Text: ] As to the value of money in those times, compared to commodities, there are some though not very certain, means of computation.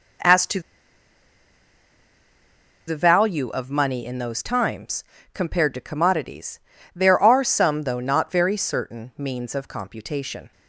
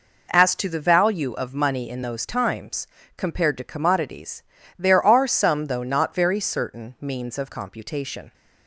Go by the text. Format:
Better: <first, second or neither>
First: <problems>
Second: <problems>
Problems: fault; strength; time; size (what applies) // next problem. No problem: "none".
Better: second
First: pauses between "to" and "the"; strong; at 0.6 s; 2.2 s long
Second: none